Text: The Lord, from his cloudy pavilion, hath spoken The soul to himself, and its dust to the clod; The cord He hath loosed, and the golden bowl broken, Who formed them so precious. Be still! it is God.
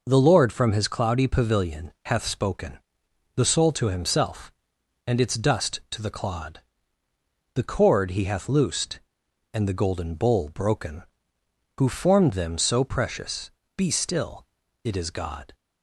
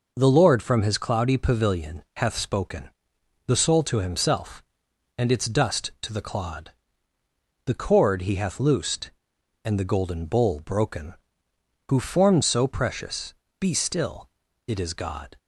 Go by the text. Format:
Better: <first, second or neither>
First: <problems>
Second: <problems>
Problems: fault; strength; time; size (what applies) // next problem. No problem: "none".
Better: first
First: pauses between "spoken" and "The"; noticeable; at 2.8 s; 0.56 s long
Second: pauses between "spoken" and "The"; noticeable; at 2.9 s; 0.56 s long // skips "them"; at 12.4 s